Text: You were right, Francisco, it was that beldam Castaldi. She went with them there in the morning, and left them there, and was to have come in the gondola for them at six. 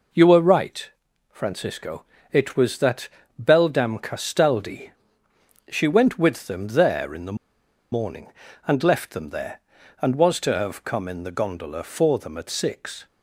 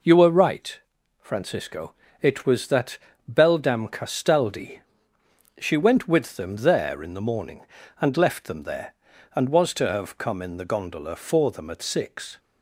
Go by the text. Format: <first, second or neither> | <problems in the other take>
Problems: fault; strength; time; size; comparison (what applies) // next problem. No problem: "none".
second | pauses between "that" and "beldam"; slight; at 3.0 s; 0.34 s long; slight in the second // pauses between "the" and "morning"; noticeable; at 7.3 s; 0.56 s long